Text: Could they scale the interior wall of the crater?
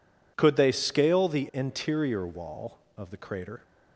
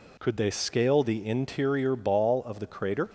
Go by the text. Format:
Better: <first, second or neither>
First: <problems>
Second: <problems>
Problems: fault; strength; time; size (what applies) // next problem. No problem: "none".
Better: first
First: none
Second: says "ball" for "wall"; at 1.9 s